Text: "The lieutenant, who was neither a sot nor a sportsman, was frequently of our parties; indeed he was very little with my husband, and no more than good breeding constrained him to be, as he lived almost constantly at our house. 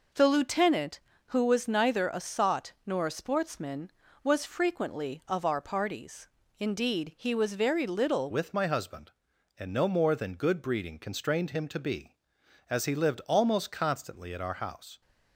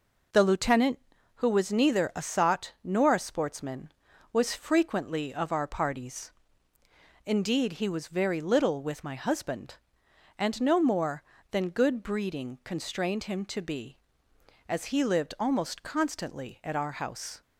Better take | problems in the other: second | changes voice at "with"; from 8.3 s on; 6.7 s long

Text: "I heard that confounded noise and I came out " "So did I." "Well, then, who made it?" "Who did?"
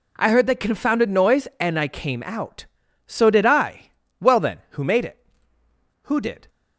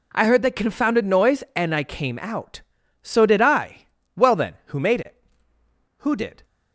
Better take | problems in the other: neither | none

